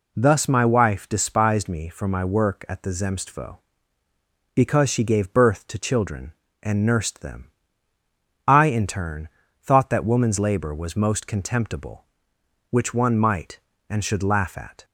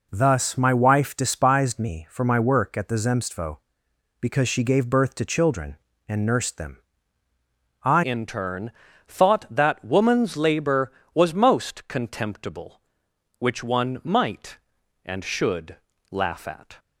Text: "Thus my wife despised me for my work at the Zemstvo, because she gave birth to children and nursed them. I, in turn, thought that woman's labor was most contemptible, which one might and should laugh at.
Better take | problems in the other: first | changes voice at "in"; from 8.0 s on; 8.7 s long // pauses between "should" and "laugh"; slight; at 15.7 s; 0.34 s long

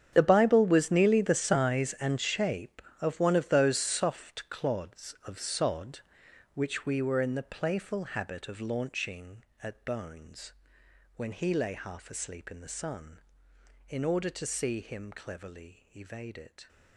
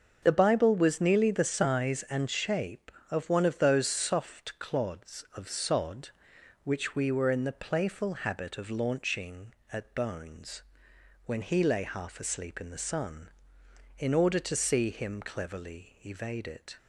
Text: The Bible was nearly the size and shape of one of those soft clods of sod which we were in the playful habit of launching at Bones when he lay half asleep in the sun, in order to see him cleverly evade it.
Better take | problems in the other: second | gets quieter; strong; throughout; 16 dB // starts louder than the rest; strong; until 1.1 s; 8.5 dB; also in the second // pauses between "Bones" and "when"; noticeable; at 10.5 s; 0.64 s long; noticeable in the second

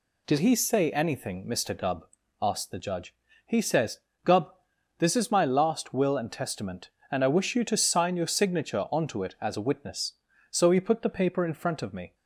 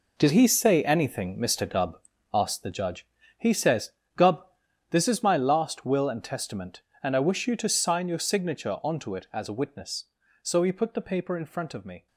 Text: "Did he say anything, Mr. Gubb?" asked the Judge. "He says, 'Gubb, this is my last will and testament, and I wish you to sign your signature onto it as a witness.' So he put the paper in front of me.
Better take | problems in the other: first | gets quieter; strong; throughout; 11 dB

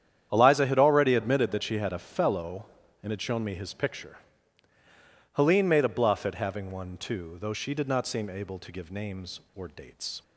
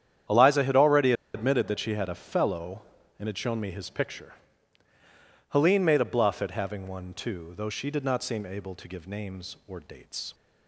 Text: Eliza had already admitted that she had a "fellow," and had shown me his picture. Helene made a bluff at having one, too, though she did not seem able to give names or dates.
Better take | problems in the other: first | starts louder than the rest; strong; until 1.5 s; 9.5 dB; strong in the first // pauses between "already" and "admitted"; slight; at 1.1 s; 0.21 s long

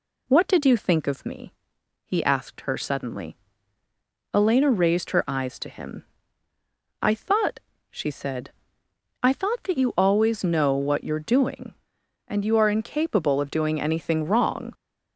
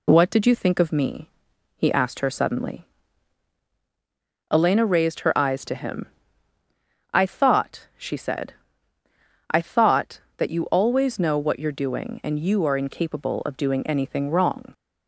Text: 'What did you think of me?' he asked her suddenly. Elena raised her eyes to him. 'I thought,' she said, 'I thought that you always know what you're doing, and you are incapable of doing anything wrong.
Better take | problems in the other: neither | none

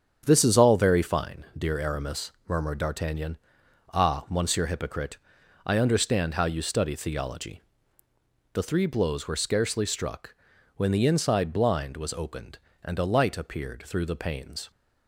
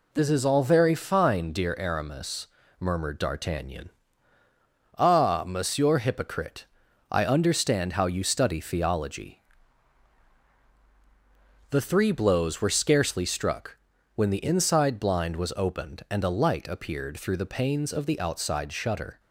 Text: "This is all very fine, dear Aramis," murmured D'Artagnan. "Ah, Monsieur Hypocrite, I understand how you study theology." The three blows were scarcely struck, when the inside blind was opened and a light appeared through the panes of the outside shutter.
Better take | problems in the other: second | starts louder than the rest; strong; until 1.2 s; 8 dB // stops before "of the outside shutter"; at 14.7 s

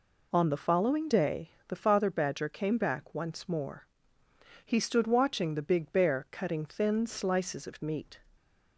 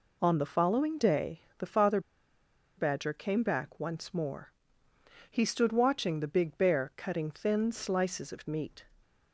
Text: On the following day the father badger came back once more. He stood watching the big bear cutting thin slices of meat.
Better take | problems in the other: first | pauses between "day" and "the"; slight; at 1.3 s; 0.20 s long; slight in the first // pauses between "father" and "badger"; noticeable; at 2.0 s; 0.75 s long

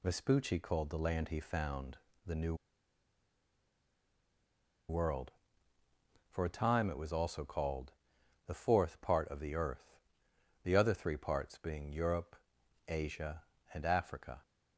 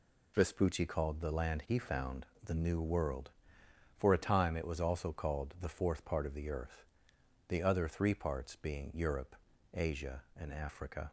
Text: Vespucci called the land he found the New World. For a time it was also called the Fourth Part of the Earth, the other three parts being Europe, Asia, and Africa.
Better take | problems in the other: second | pauses between "found" and "the"; slight; at 1.9 s; 0.26 s long; slight in the second // pauses between "New" and "World"; strong; at 2.5 s; 2.3 s long // pauses between "called" and "the"; noticeable; at 7.9 s; 0.54 s long

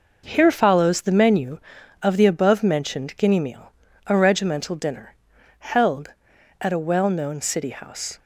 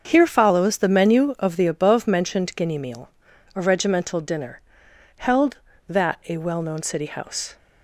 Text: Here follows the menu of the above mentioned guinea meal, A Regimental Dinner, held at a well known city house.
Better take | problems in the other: first | starts louder than the rest; until 1.0 s; 6.5 dB // says "that" for "at"; at 5.8 s

